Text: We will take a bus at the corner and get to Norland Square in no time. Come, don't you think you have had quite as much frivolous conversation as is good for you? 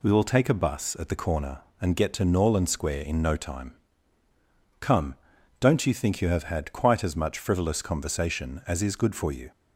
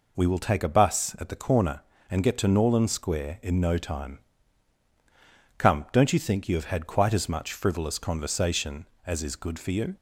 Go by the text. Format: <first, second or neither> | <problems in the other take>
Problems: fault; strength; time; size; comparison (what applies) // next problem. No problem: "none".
neither | none